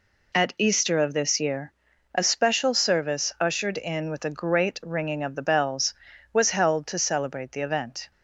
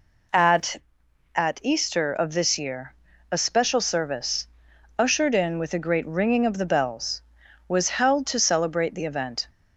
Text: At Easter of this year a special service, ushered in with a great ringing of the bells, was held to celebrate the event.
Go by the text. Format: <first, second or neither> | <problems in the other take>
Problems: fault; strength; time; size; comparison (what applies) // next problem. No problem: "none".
first | says "At" twice; at 1.3 s // pauses between "year" and "a"; at 2.9 s; 0.38 s long; also in the first